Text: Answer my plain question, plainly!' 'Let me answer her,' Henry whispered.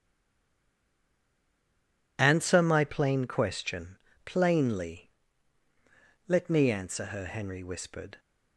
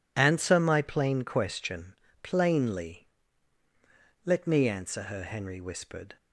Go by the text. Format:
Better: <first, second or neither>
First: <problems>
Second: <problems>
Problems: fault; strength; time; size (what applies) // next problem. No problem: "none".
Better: second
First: stays silent before the first word; until 2.1 s; 2.1 s long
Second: none